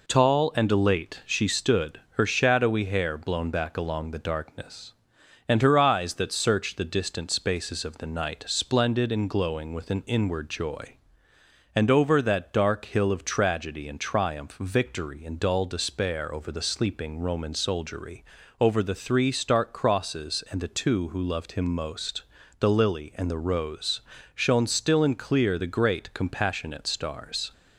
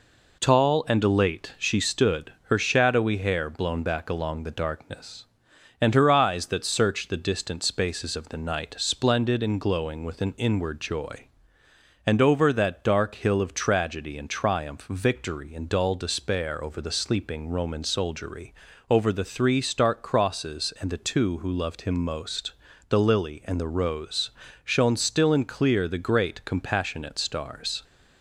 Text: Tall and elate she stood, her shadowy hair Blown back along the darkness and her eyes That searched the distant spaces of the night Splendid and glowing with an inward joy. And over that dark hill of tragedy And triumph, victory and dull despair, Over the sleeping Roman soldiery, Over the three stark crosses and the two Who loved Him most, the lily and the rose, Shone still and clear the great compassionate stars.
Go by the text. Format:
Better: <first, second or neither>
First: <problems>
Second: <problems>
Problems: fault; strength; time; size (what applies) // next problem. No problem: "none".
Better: neither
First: none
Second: none